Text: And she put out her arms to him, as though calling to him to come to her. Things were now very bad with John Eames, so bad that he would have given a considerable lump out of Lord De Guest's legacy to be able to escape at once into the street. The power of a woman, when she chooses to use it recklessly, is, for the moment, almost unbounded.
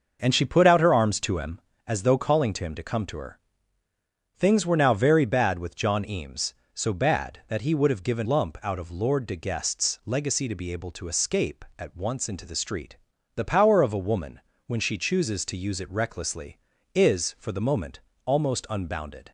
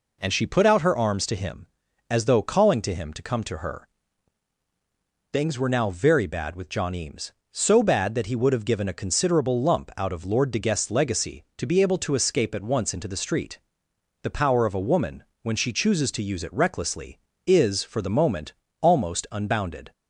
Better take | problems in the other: second | starts louder than the rest; noticeable; until 1.2 s; 6 dB // skips "a considerable"; at 8.2 s

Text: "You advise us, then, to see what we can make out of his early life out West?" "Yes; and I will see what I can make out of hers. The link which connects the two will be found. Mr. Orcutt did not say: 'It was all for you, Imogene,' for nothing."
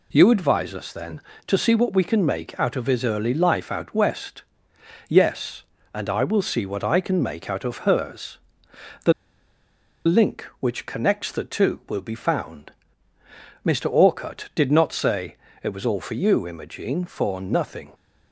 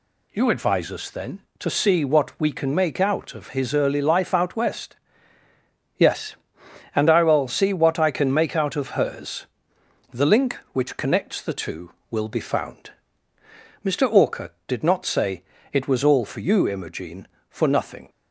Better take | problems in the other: second | pauses between "The" and "link"; noticeable; at 9.1 s; 0.93 s long

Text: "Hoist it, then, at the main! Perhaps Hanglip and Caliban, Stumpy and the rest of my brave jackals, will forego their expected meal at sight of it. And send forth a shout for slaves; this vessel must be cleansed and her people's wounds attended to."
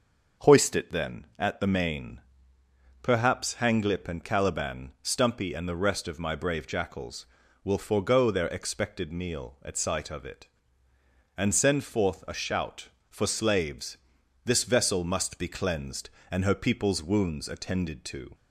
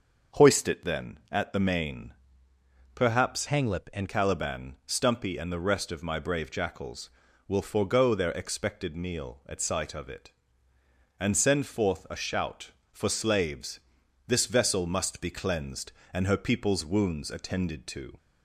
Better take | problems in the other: first | starts louder than the rest; noticeable; until 1.4 s; 6 dB // changes voice from "Hanglip" to "and"; from 3.4 to 4.0 s; 0.6 s long

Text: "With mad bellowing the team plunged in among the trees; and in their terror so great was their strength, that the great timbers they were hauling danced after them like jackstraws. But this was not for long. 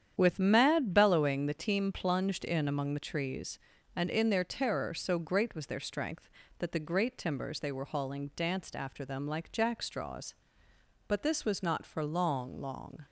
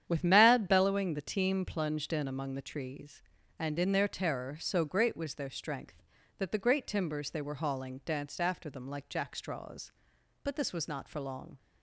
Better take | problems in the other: second | starts louder than the rest; strong; until 1.1 s; 9 dB; strong in the second // says "long" twice; at 12.5 s

